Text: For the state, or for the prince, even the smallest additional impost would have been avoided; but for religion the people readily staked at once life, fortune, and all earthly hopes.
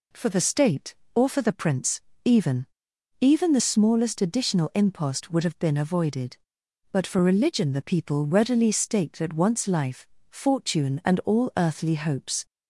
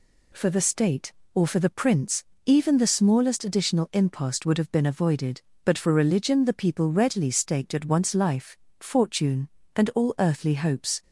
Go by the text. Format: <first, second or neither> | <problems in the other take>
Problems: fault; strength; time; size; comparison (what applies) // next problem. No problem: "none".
second | says "even" twice; at 3.2 s